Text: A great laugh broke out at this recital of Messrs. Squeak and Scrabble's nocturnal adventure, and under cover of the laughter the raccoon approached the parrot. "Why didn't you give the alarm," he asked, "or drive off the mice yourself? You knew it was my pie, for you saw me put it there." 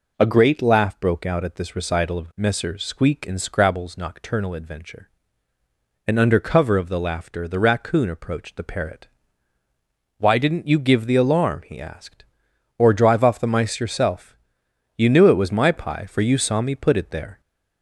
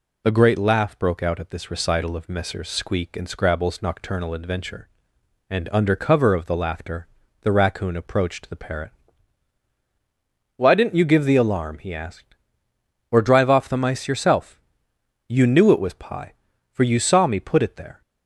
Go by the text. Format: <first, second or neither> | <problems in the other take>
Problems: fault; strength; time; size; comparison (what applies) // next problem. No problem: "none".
first | pauses between "laughter" and "the"; slight; at 7.0 s; 0.34 s long // skips "my"; at 15.9 s